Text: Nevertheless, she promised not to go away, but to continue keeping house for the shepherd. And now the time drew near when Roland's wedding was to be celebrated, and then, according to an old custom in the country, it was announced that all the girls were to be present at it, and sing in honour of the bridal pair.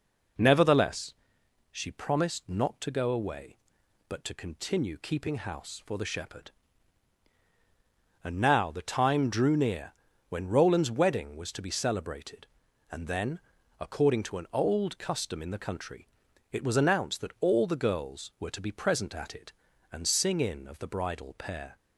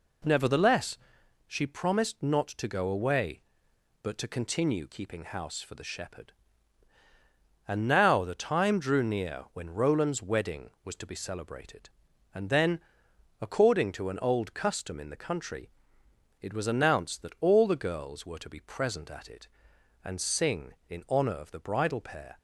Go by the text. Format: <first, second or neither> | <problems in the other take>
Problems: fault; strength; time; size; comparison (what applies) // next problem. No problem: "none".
second | pauses between "near" and "when"; at 9.9 s; 0.38 s long // skips "honour"; at 20.6 s